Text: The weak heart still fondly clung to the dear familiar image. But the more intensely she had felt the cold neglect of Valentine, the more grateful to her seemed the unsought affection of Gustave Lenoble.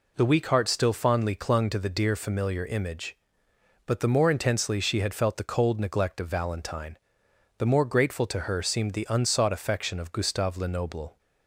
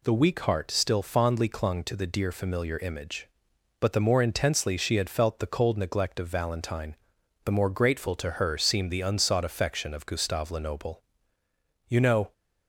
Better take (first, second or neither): first